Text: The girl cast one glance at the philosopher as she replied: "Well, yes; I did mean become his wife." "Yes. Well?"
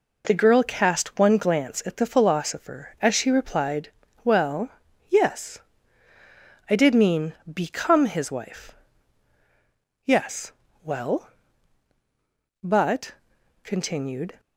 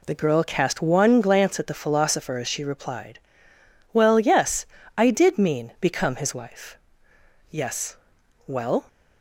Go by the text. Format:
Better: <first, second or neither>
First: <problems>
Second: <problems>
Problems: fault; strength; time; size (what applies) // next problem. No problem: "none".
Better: second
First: goes on to say "But continued"; strong; from 12.6 s on; 1.7 s long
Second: none